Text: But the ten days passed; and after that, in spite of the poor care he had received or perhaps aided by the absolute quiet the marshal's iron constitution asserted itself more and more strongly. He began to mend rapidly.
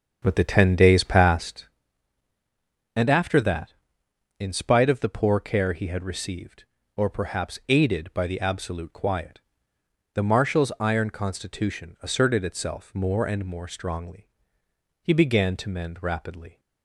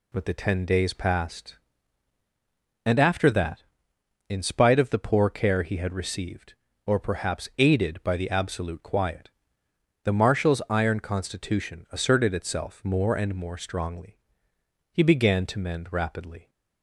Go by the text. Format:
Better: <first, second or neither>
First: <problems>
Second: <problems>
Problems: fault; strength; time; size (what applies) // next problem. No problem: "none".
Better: second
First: starts louder than the rest; until 1.7 s; 7 dB // pauses between "quiet" and "the"; noticeable; at 9.3 s; 0.74 s long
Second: pauses between "quiet" and "the"; noticeable; at 9.2 s; 0.74 s long